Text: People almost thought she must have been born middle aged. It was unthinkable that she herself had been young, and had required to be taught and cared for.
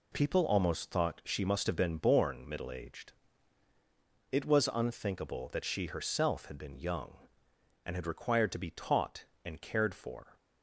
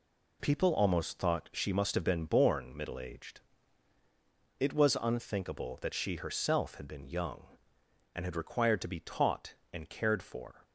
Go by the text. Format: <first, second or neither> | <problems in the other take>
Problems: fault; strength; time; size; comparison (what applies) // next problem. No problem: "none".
neither | none